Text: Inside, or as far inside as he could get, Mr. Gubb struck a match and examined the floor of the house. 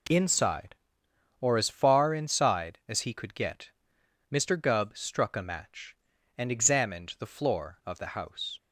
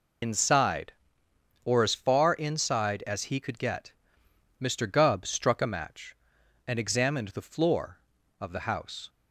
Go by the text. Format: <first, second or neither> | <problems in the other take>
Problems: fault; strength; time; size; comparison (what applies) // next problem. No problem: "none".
first | loses the start of "Inside"; at 0.2 s; 95 ms